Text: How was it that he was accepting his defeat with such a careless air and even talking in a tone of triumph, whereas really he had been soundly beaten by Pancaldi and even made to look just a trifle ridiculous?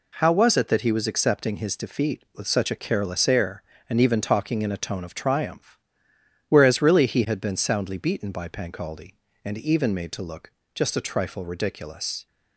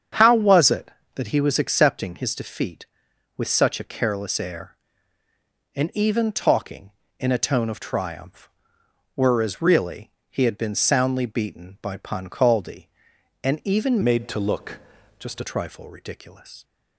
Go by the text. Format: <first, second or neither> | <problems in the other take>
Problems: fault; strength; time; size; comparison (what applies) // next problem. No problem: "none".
first | starts louder than the rest; strong; until 1.4 s; 7.5 dB // pauses between "really" and "he"; slight; at 10.1 s; 0.18 s long // changes voice from "made" to "a"; from 14.0 to 15.4 s; 1.4 s long // pauses between "look" and "just"; at 14.7 s; 0.40 s long; slight in the first